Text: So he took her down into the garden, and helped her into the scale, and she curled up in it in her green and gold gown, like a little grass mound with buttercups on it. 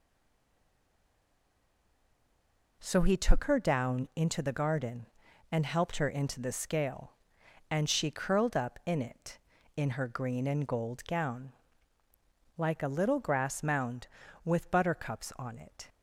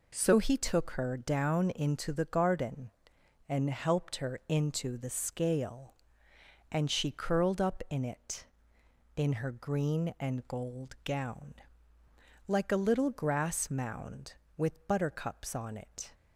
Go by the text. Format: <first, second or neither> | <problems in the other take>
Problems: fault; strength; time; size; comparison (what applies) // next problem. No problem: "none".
second | stays silent before the first word; strong; until 2.8 s; 2.8 s long